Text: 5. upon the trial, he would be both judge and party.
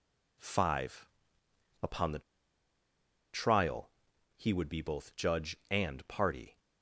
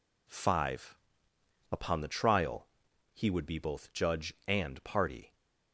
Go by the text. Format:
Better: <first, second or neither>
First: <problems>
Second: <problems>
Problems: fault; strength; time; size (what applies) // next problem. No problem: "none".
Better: second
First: pauses between "the" and "trial"; at 2.1 s; 1.1 s long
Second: none